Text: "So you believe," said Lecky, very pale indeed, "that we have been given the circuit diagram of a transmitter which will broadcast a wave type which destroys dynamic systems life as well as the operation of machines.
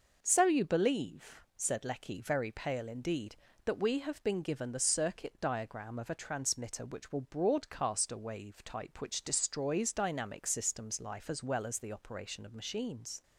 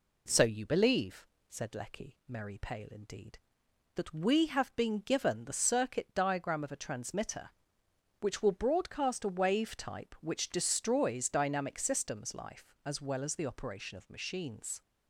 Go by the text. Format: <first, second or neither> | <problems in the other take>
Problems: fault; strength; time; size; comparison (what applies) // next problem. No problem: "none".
first | says "merry" for "very"; at 2.2 s